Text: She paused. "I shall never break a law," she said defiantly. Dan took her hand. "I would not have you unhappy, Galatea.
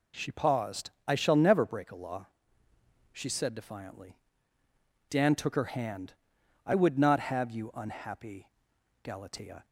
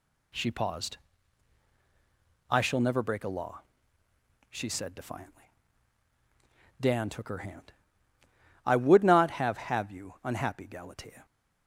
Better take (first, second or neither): first